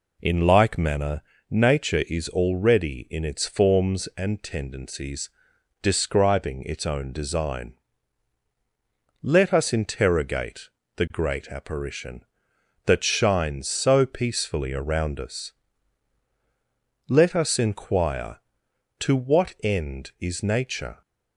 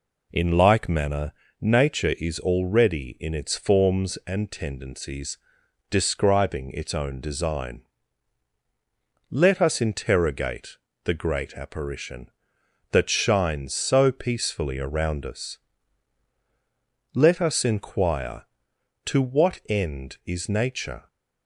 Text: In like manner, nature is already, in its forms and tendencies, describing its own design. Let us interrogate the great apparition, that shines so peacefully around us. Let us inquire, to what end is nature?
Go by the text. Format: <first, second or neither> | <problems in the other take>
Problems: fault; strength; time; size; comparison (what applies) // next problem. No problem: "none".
neither | pauses between "interrogate" and "the"; slight; the same in both